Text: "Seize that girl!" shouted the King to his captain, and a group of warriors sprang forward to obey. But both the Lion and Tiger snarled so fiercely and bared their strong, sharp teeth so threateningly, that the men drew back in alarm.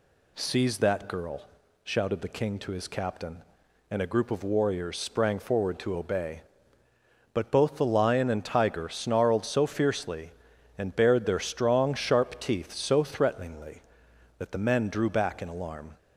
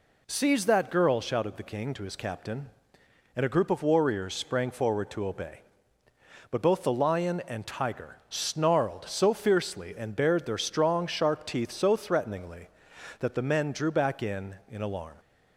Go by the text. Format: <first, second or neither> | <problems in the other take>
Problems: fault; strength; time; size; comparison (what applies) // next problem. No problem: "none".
first | says "in" twice; at 14.6 s